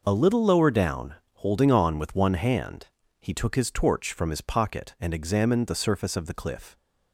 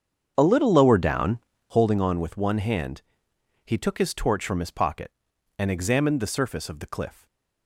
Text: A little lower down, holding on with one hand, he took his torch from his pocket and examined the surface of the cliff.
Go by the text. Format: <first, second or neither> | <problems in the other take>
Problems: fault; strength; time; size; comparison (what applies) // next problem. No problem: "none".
first | starts louder than the rest; strong; until 1.9 s; 7.5 dB // stays silent after the last word; slight; from 7.1 s on; 0.5 s long